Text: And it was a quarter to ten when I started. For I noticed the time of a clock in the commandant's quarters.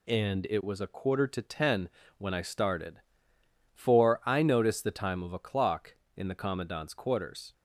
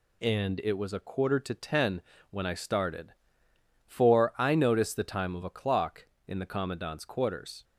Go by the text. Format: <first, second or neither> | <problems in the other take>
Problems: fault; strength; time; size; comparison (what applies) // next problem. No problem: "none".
neither | pauses between "ten" and "when"; slight; the same in both